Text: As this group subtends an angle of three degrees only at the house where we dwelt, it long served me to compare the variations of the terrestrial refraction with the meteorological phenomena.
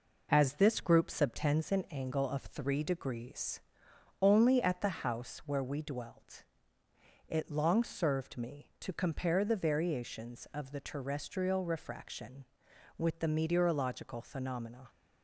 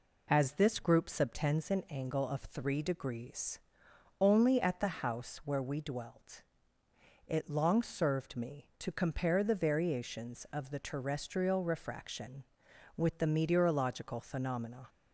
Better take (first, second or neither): second